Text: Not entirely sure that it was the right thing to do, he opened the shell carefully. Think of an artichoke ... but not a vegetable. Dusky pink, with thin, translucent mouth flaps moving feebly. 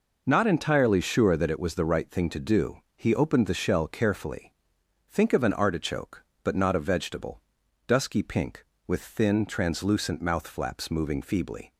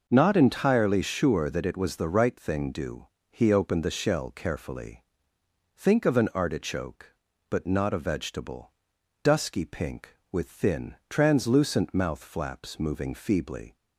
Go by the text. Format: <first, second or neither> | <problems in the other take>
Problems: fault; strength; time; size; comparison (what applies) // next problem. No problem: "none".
first | skips "to"; at 2.7 s